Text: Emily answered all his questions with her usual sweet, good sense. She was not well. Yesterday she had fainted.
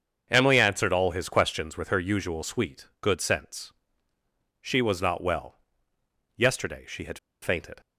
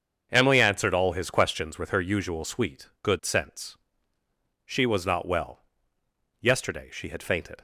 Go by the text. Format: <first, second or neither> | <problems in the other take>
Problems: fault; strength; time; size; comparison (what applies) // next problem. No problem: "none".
second | starts louder than the rest; until 1.3 s; 7 dB; also in the second // pauses between "had" and "fainted"; slight; at 7.1 s; 0.23 s long